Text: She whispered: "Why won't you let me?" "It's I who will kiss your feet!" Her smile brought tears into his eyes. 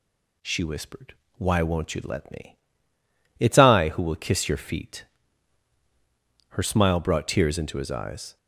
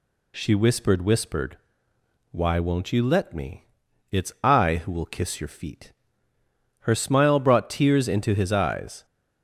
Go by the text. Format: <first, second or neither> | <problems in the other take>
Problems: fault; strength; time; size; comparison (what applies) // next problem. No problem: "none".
first | says "whispered" twice; at 1.0 s